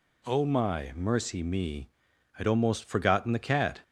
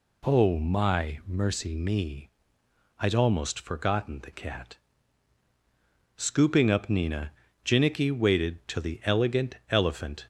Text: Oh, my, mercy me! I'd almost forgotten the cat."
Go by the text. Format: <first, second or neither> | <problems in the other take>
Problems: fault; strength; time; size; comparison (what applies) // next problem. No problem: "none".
first | goes on to say "Scooping up Nina Jinnicky waited till the Elegant Elephant"; strong; from 6.1 s on; 4.1 s long